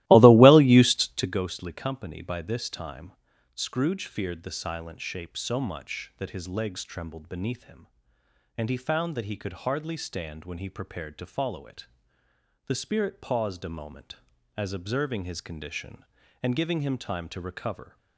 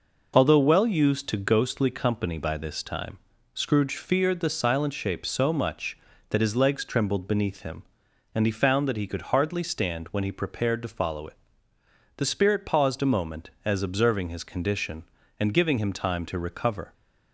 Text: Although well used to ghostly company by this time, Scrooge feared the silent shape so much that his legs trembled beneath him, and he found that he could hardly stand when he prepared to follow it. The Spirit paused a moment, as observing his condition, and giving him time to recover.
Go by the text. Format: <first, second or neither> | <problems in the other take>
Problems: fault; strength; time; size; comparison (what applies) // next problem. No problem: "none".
second | starts louder than the rest; strong; until 1.3 s; 17 dB